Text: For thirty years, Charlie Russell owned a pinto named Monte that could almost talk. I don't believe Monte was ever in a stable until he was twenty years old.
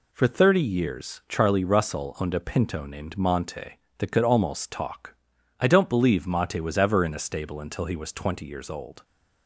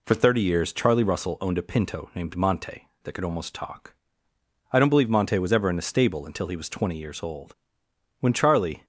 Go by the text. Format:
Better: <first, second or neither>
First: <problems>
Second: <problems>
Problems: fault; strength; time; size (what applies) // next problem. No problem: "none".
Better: first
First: none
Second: goes on to say "When Charlie"; noticeable; from 8.2 s on; 0.64 s long